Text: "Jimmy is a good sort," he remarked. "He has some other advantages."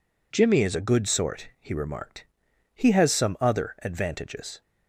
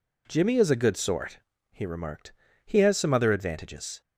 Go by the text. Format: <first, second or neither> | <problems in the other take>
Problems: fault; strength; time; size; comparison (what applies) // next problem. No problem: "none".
neither | none